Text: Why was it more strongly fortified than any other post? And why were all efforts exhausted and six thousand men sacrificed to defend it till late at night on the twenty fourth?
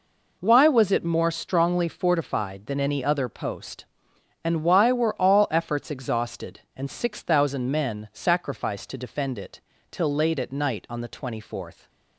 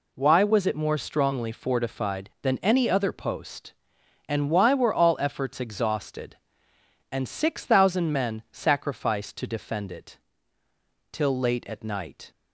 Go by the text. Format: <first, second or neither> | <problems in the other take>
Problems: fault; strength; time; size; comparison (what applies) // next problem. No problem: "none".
first | pauses between "it" and "till"; noticeable; at 10.1 s; 0.94 s long; slight in the first // stops before "on the twenty fourth"; at 12.3 s